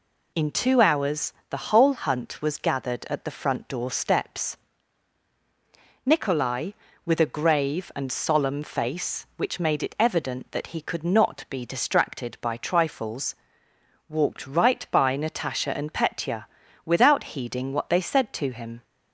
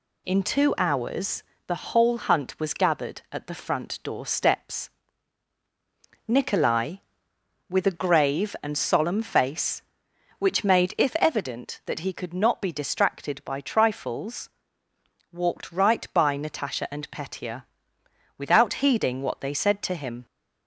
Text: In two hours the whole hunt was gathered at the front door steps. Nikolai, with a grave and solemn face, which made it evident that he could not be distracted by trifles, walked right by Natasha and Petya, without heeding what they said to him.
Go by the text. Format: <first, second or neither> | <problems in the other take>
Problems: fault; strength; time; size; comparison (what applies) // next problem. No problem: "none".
first | pauses between "hours" and "the"; slight; at 1.4 s; 0.24 s long; slight in the first // says "if" for "it"; at 10.9 s